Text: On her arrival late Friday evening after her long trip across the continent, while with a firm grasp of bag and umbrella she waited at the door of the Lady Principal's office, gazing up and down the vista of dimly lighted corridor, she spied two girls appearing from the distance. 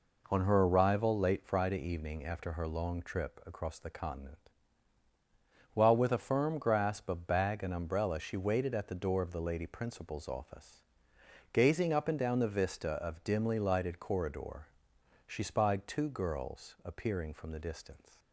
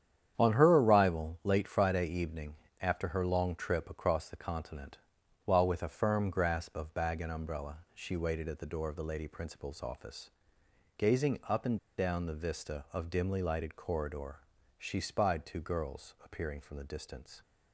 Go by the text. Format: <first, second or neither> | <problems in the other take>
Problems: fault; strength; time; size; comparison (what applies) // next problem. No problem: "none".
first | starts louder than the rest; strong; until 1.3 s; 9 dB // pauses between "evening" and "after"; slight; at 2.5 s; 0.26 s long // pauses between "umbrella" and "she"; slight; at 7.7 s; 0.16 s long // pauses between "and" and "down"; slight; at 11.7 s; 0.19 s long